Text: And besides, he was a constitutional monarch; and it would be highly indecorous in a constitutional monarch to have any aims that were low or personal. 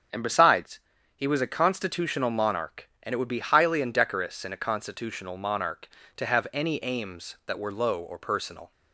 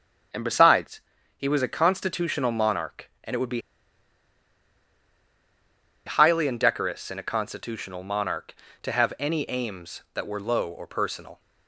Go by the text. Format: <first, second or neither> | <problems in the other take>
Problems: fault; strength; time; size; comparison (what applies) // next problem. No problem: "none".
first | starts louder than the rest; strong; until 1.6 s; 7 dB; also in the first // pauses between "be" and "highly"; strong; at 3.6 s; 2.4 s long